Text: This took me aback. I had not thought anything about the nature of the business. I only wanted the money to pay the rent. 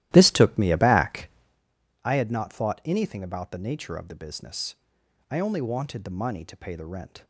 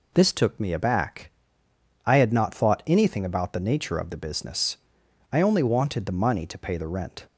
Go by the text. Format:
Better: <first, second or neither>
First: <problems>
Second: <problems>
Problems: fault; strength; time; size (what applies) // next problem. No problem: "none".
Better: second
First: starts louder than the rest; strong; until 1.6 s; 14.5 dB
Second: none